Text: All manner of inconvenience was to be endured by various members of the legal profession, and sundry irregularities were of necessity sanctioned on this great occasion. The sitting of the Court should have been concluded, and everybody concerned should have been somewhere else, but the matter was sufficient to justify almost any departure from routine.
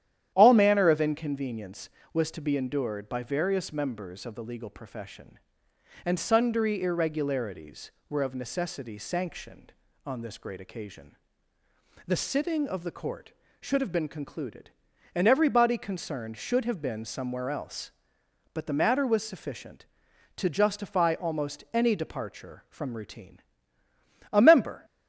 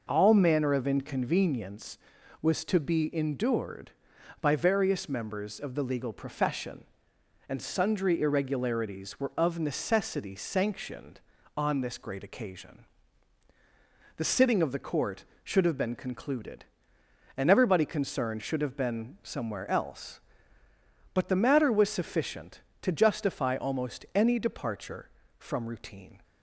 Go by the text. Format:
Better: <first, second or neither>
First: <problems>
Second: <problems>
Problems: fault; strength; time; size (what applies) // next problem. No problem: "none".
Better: second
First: starts louder than the rest; strong; until 1.3 s; 11 dB // goes on to say "A member"; from 24.3 s on; 0.52 s long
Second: none